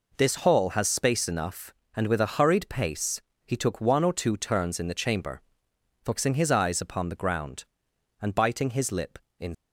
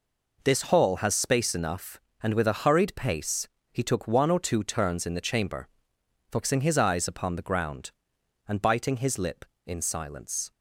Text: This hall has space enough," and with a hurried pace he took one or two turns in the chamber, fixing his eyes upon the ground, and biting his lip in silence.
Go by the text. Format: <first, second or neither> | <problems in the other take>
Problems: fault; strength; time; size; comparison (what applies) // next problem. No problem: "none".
second | pauses between "pace" and "he"; slight; at 3.2 s; 0.26 s long; slight in the second // stops before "silence"; at 9.5 s